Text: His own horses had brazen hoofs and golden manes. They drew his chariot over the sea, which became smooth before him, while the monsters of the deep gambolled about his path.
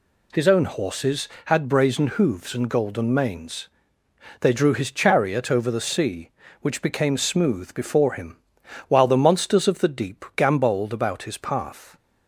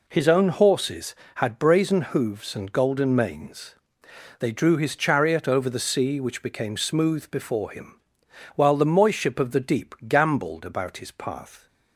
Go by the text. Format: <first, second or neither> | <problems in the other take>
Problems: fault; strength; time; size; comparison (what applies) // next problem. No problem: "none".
first | says "moiship" for "monsters"; at 8.8 s